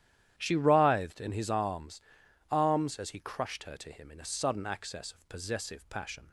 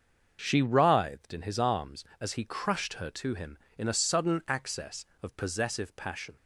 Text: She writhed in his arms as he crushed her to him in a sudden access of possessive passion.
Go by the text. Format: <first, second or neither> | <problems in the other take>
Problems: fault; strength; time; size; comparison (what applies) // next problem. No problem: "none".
second | starts louder than the rest; strong; until 1.3 s; 11 dB; also in the second // says "arms" twice; at 2.5 s